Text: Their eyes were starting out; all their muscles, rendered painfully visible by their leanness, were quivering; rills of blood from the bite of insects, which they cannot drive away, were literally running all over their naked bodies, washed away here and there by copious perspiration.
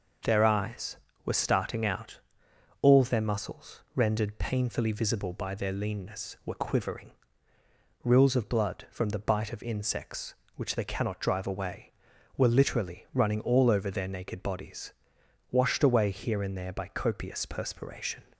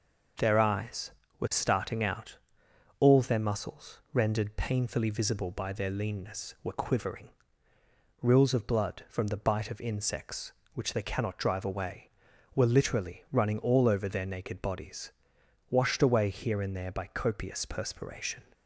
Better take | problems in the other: neither | none

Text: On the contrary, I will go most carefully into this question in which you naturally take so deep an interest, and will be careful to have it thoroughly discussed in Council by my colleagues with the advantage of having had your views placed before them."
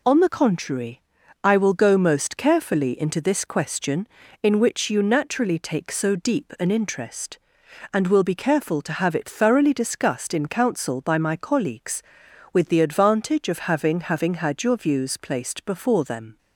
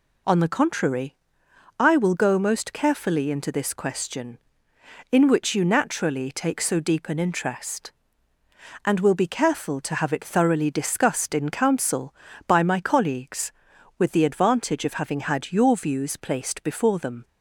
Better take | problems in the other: second | says "having" twice; at 13.9 s

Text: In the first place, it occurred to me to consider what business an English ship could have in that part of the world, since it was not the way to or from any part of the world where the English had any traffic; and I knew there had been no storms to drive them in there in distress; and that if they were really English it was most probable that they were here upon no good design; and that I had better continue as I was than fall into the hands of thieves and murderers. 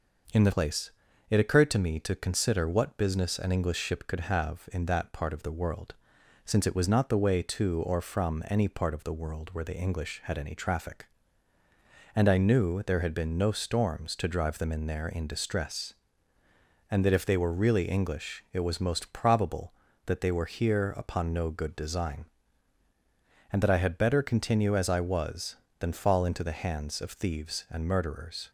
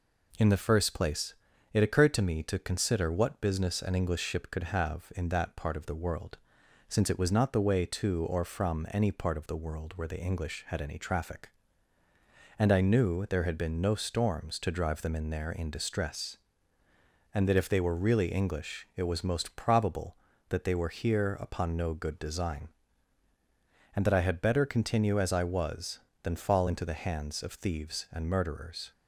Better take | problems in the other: second | skips "first"; at 0.5 s

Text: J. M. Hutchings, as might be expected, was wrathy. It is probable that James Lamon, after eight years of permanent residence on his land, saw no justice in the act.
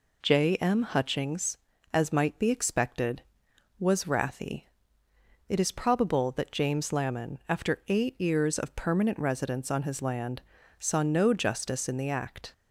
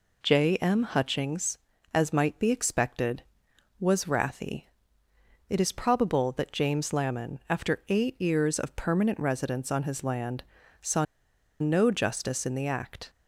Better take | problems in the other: first | pauses between "saw" and "no"; noticeable; at 11.0 s; 0.55 s long

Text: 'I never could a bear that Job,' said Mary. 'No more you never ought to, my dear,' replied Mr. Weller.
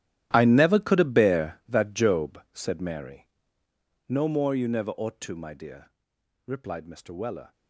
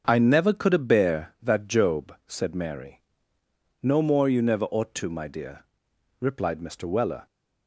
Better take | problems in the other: second | gets quieter; strong; throughout; 16.5 dB // starts louder than the rest; strong; until 1.3 s; 12.5 dB; also in the second

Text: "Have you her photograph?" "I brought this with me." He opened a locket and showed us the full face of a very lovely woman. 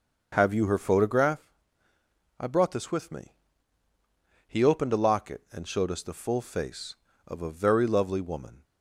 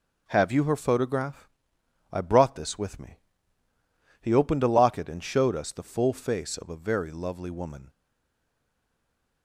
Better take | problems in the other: first | starts louder than the rest; noticeable; until 1.2 s; 6 dB // stays silent after the last word; noticeable; from 7.8 s on; 1.6 s long

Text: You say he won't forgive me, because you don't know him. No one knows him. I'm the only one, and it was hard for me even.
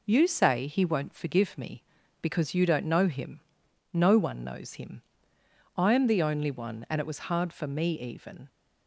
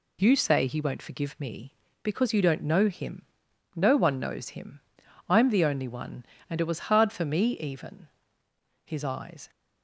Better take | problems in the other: first | goes on to say "His eyes"; noticeable; from 8.8 s on; 0.66 s long

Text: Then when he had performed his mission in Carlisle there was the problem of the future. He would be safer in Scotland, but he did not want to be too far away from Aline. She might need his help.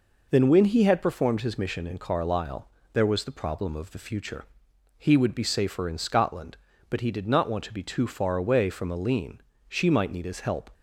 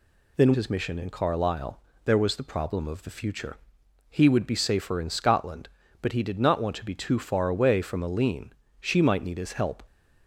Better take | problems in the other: first | skips "when he had performed"; at 0.5 s // pauses between "Carlisle" and "there"; slight; at 1.7 s; 0.26 s long; slight in the first

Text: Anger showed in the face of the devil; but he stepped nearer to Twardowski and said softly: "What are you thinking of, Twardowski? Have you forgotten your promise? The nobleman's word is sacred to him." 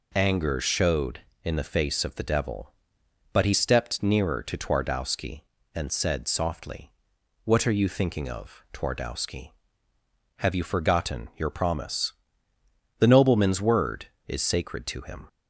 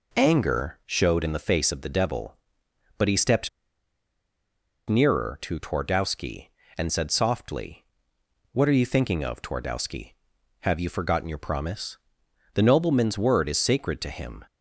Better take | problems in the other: first | pauses between "stepped" and "nearer"; strong; at 3.4 s; 1.3 s long

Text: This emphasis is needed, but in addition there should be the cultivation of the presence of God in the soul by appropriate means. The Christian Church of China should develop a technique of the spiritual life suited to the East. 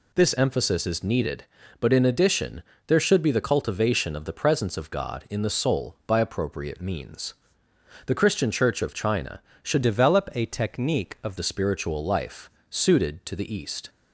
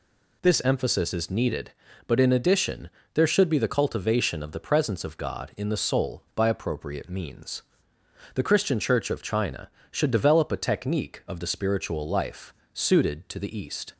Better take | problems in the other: second | pauses between "addition" and "there"; slight; at 2.6 s; 0.24 s long; slight in the second // changes voice from "develop" to "of"; from 9.8 to 11.3 s; 1.5 s long // pauses between "life" and "suited"; slight; at 12.5 s; 0.18 s long; slight in the second

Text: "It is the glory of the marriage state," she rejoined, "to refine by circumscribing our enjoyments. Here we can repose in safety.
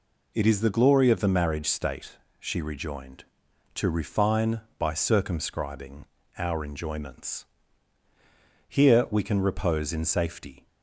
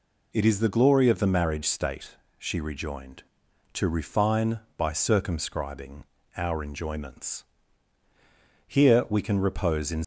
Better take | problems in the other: first | pauses between "circumscribing" and "our"; slight; at 6.0 s; 0.32 s long; slight in the first // stops before "safety"; at 10.0 s

